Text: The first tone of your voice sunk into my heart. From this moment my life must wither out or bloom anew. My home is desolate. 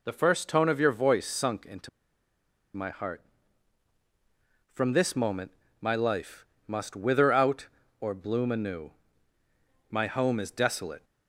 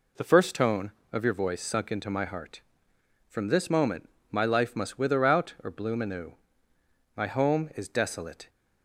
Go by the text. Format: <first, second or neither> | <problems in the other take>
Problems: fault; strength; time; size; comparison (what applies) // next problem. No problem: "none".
second | pauses between "into" and "my"; noticeable; at 1.8 s; 0.86 s long // pauses between "moment" and "my"; slight; at 5.5 s; 0.28 s long; slight in the second // pauses between "life" and "must"; slight; at 6.4 s; 0.24 s long